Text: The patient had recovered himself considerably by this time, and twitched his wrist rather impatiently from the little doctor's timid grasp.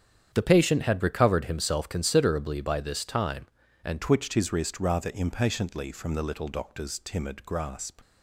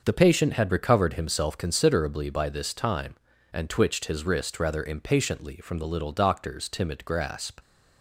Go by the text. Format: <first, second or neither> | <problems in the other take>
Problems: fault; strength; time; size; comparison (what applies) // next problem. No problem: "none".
second | starts louder than the rest; strong; until 1.3 s; 8.5 dB; also in the second // changes voice at "twitched"; from 4.0 s on; 4.0 s long